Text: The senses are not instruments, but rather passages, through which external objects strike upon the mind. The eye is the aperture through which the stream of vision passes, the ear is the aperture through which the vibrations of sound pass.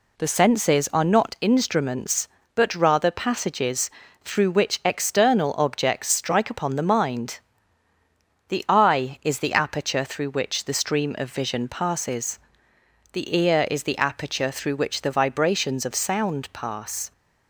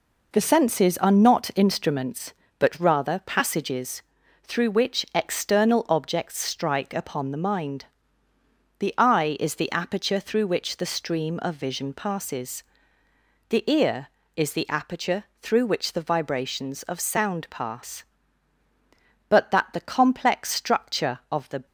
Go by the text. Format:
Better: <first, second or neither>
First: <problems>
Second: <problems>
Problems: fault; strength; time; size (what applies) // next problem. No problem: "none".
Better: first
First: none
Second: pauses between "aperture" and "through"; slight; at 15.2 s; 0.16 s long // goes on to say "But that the complex structure of the"; strong; from 19.2 s on; 2.3 s long